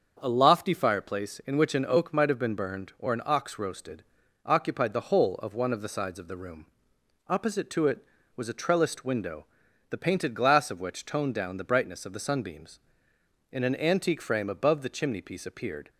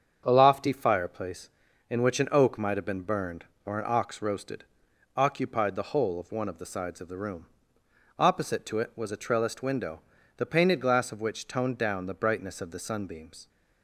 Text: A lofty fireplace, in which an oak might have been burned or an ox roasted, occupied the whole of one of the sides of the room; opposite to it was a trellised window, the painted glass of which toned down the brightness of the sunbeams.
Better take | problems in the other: second | starts louder than the rest; until 1.2 s; 6.5 dB; also in the second // goes on to say "In an antique frame above the chimney piece appeared"; strong; from 13.5 s on; 2.3 s long

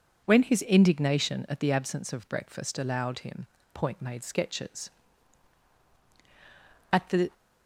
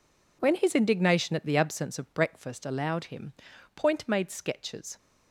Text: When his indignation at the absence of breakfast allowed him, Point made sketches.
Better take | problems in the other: second | goes on to say "At the"; slight; from 6.9 s on; 0.42 s long

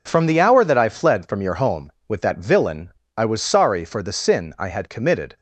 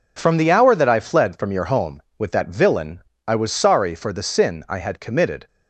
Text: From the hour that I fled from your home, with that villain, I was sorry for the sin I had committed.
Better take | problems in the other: neither | none

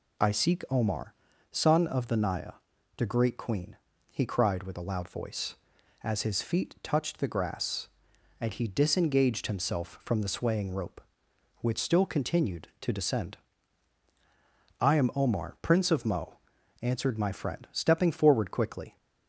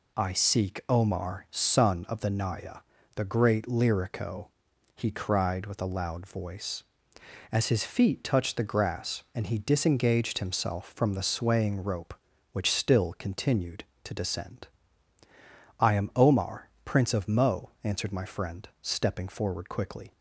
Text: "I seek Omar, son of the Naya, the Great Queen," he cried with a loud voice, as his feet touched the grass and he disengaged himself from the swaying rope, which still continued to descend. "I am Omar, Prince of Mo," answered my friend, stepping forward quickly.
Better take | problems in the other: first | says "Lyrico" for "Queen"; at 3.6 s

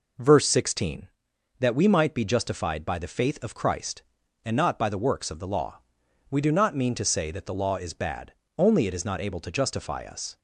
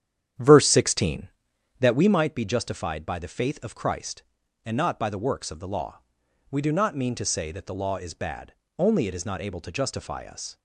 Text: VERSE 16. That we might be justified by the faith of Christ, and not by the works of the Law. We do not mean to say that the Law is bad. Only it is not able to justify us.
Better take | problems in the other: first | starts louder than the rest; strong; until 2.2 s; 9.5 dB

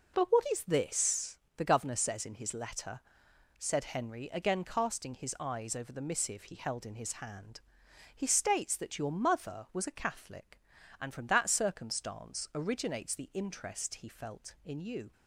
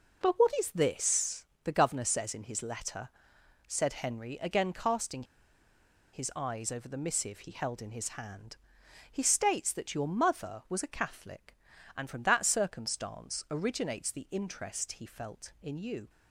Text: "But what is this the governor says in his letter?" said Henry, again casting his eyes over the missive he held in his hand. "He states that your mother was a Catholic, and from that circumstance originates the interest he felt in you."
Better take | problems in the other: first | pauses between "this" and "the"; slight; at 1.4 s; 0.18 s long; slight in the first // pauses between "casting" and "his"; noticeable; at 5.2 s; 0.89 s long

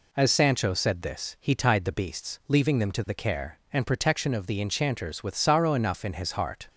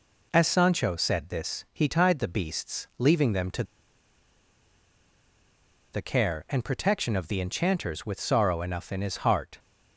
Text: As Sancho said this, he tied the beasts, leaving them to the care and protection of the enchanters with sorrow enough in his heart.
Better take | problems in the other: first | pauses between "to" and "the"; strong; at 3.6 s; 2.2 s long

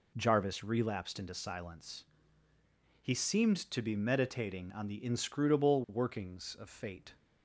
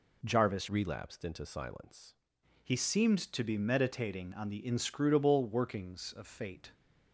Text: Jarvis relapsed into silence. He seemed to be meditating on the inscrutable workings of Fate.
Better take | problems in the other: first | changes voice from "relapsed" to "silence"; from 0.6 to 2.1 s; 1.5 s long

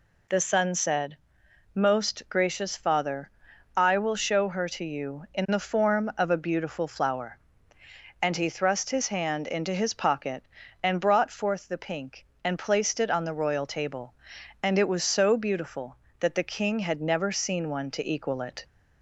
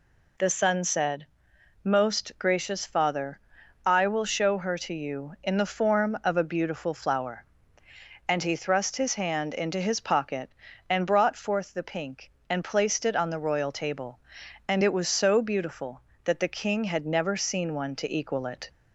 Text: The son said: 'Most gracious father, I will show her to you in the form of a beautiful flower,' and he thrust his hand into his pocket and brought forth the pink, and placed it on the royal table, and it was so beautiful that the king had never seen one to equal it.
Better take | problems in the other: neither | none

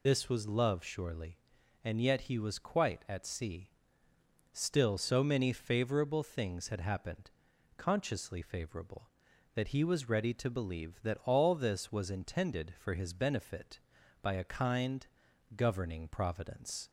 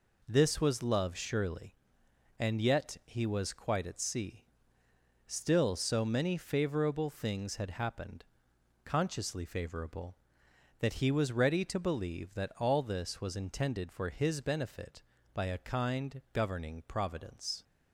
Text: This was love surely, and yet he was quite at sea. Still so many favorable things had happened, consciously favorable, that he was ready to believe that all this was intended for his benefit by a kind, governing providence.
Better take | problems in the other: second | loses the start of "This"; at 0.0 s; 50 ms

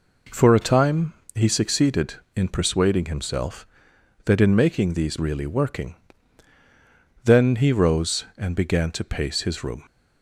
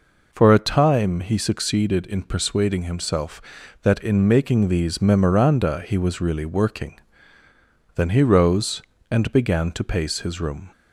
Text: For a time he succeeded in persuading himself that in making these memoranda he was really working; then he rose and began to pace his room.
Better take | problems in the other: second | pauses between "time" and "he"; slight; at 1.1 s; 0.20 s long // skips "memoranda he was"; at 5.1 s

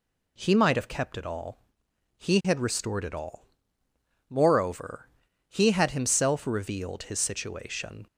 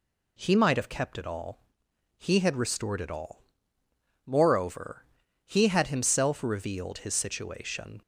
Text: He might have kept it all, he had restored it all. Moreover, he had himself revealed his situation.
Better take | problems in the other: neither | none

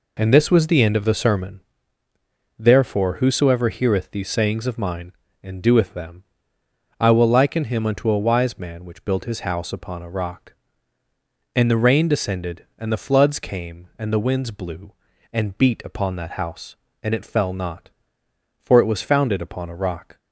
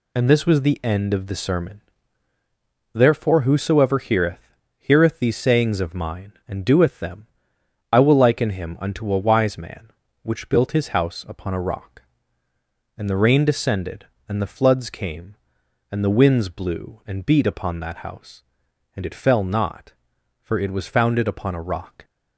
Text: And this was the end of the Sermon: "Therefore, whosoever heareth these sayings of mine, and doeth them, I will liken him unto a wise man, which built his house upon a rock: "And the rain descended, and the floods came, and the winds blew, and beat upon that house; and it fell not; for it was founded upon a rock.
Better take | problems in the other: first | says "heareth" twice; at 4.7 s

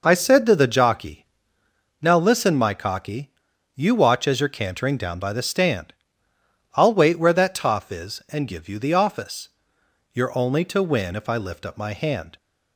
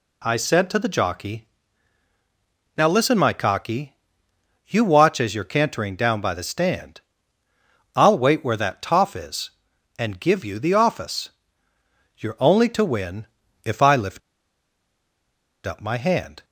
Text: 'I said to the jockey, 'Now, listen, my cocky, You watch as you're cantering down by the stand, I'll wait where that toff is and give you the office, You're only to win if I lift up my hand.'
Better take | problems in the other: first | pauses between "win" and "if"; at 13.2 s; 0.38 s long // pauses between "lift" and "up"; strong; at 14.2 s; 1.4 s long

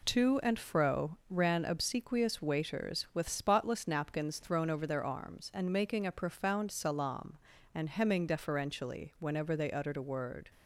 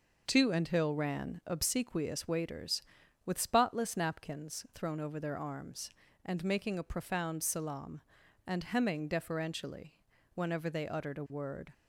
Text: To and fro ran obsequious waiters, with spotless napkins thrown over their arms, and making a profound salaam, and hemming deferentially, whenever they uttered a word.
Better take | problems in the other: first | says "hill" for "fro"; at 0.6 s

